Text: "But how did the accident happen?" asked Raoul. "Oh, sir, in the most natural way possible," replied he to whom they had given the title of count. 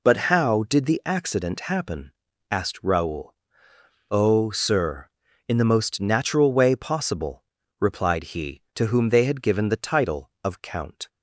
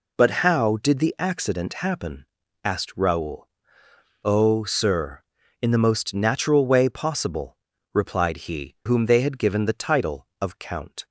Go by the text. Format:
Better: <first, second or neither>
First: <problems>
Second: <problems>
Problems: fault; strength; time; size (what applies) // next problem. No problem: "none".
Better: first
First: none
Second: skips "to"; at 8.7 s